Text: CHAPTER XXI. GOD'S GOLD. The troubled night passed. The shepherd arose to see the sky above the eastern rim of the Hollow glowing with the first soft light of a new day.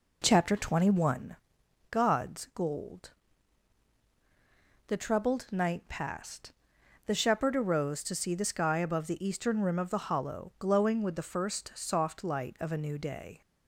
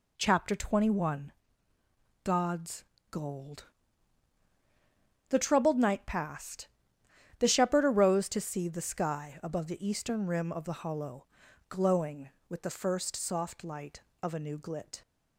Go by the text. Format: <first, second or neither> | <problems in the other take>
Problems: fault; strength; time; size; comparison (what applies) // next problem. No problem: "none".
first | pauses between "GOD'S" and "GOLD"; slight; at 2.8 s; 0.26 s long // pauses between "Hollow" and "glowing"; at 11.2 s; 0.42 s long // says "glit" for "day"; at 14.5 s